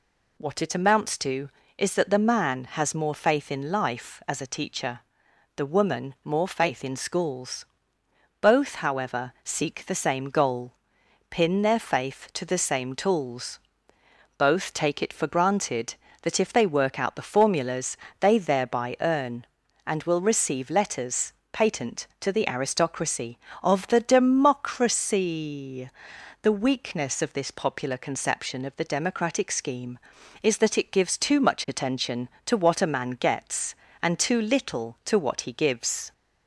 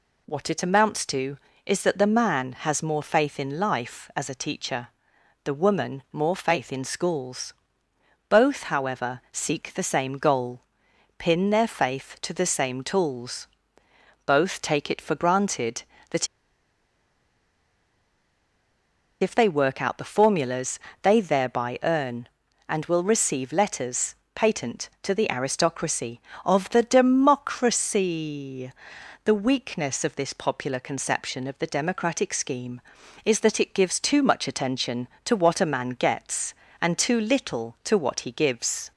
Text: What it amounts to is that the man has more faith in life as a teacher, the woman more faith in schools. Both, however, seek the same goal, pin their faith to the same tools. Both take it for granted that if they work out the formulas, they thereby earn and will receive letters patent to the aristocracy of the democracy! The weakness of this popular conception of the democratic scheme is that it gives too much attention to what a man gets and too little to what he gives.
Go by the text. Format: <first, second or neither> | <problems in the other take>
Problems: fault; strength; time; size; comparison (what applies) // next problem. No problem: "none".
first | pauses between "that" and "if"; strong; at 16.2 s; 2.9 s long // pauses between "letters" and "patent"; slight; at 24.1 s; 0.18 s long; slight in the first